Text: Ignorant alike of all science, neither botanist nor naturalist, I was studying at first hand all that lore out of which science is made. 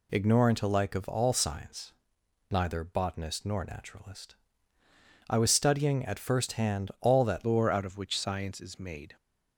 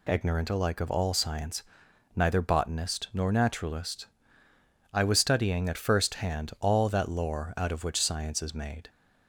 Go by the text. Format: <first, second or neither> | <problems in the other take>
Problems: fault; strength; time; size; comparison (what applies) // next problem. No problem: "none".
second | changes voice at "lore"; from 7.4 s on; 1.7 s long